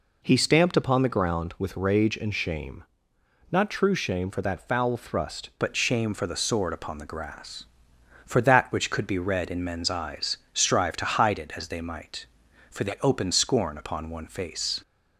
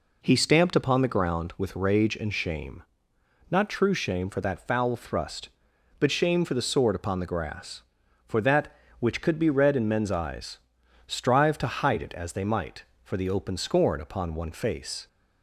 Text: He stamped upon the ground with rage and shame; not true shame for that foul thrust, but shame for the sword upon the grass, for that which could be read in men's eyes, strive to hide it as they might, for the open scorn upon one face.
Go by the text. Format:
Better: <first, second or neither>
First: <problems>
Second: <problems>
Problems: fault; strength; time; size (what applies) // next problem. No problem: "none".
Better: second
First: changes voice at "but"; from 5.5 s on; 9.3 s long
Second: none